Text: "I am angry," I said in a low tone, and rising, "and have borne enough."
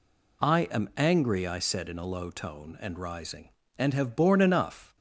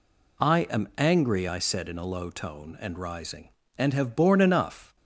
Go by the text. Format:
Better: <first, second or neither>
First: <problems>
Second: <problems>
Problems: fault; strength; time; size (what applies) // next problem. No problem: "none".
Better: neither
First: none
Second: none